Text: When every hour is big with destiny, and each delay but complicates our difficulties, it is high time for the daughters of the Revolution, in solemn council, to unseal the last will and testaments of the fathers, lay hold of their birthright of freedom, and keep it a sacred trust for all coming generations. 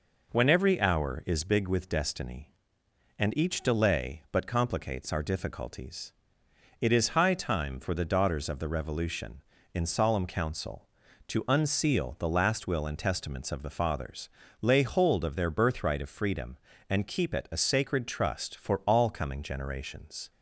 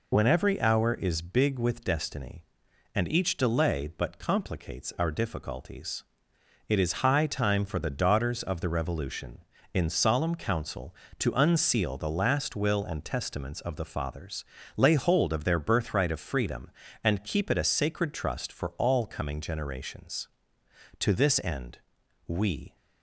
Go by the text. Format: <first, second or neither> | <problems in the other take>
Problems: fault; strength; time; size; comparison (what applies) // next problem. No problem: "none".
first | goes on to say "To this end we"; strong; from 21.0 s on; 1.7 s long